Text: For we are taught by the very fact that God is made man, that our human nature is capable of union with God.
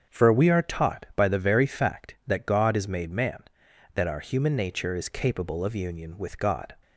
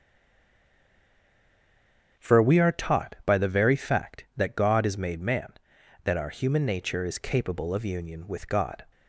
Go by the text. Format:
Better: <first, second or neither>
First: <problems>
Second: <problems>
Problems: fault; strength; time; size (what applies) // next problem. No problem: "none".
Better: first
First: starts louder than the rest; strong; until 1.2 s; 7.5 dB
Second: stays silent before the first word; until 2.1 s; 2.1 s long // starts louder than the rest; strong; until 3.3 s; 7.5 dB